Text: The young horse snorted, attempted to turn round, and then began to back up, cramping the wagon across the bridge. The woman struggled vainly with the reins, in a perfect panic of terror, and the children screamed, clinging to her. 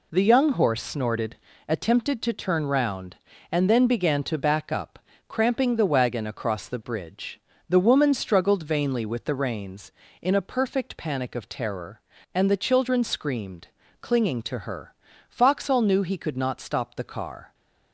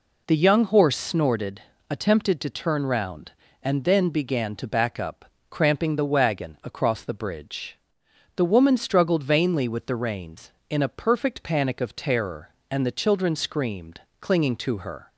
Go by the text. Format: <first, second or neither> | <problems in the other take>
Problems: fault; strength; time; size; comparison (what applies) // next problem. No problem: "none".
second | goes on to say "Foxhall knew he could not stop the car"; strong; from 15.2 s on; 2.2 s long